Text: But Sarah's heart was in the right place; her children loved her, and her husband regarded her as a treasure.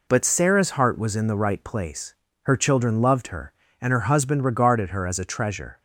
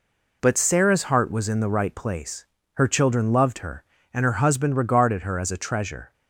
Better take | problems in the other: neither | none

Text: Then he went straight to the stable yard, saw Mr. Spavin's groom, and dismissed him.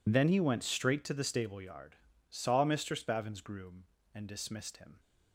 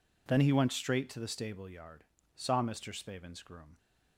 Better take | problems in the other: first | stops before "and dismissed him"; at 3.7 s

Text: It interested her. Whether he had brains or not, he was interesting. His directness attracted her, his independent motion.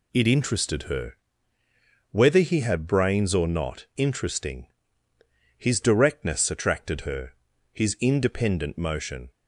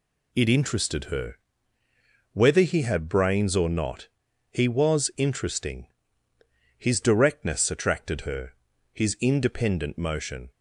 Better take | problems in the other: second | skips "he was"; at 3.9 s

